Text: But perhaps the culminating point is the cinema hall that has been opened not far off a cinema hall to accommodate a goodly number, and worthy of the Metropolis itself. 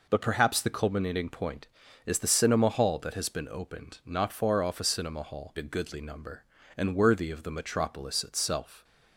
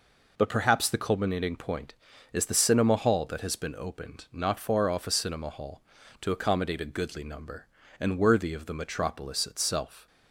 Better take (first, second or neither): second